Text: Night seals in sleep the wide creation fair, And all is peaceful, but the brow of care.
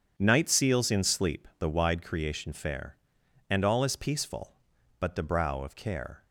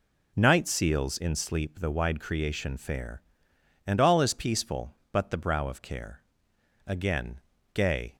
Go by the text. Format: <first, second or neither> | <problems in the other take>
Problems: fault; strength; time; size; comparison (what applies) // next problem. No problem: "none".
first | goes on to say "Again gay"; noticeable; from 6.8 s on; 1.2 s long